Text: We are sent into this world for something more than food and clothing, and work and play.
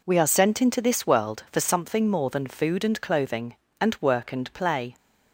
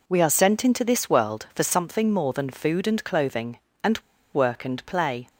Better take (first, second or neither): first